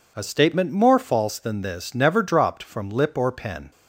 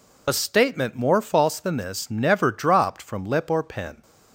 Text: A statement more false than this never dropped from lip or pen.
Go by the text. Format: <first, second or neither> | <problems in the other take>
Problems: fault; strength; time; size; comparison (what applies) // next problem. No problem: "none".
first | loses the start of "A"; at 0.2 s; 60 ms